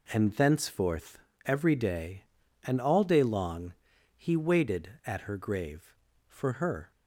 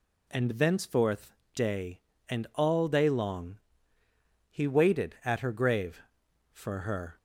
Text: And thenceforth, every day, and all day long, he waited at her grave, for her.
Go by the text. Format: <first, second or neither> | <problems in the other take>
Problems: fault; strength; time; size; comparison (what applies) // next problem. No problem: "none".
first | skips "every"; at 1.4 s